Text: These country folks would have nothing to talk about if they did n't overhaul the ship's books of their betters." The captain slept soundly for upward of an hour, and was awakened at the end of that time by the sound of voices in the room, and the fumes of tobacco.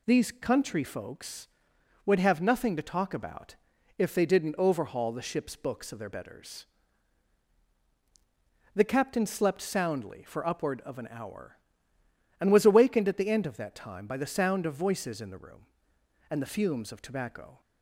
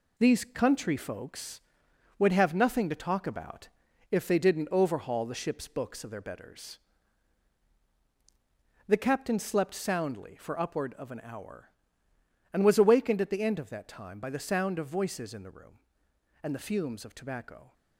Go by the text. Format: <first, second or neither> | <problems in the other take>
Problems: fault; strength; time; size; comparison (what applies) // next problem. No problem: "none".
first | gets quieter; noticeable; throughout; 6 dB // pauses between "about" and "if"; at 3.6 s; 0.42 s long; also in the first